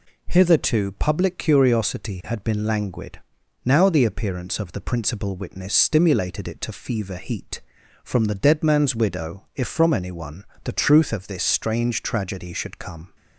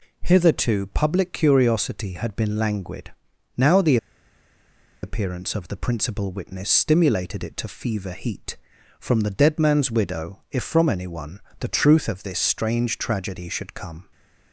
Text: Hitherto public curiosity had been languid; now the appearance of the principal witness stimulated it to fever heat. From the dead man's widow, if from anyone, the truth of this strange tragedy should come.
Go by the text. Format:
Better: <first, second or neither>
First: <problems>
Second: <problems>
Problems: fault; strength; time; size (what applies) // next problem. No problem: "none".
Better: first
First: none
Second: pauses between "the" and "appearance"; at 3.9 s; 1.0 s long